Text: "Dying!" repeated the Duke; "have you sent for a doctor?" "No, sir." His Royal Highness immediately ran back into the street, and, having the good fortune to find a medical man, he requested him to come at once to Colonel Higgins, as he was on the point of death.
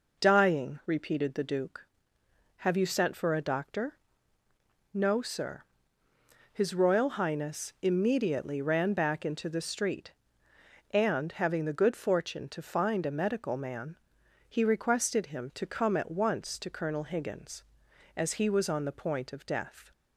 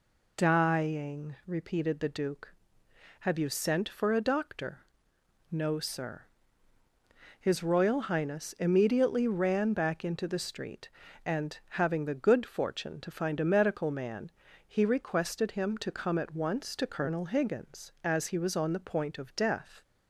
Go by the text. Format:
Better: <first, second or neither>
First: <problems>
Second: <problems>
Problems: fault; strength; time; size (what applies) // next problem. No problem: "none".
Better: neither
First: none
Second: none